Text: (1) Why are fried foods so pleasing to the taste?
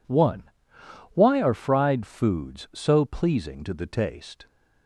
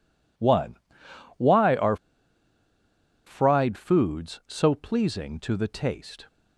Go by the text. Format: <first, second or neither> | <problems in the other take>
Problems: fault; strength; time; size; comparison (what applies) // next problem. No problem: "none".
first | pauses between "are" and "fried"; strong; at 1.9 s; 1.3 s long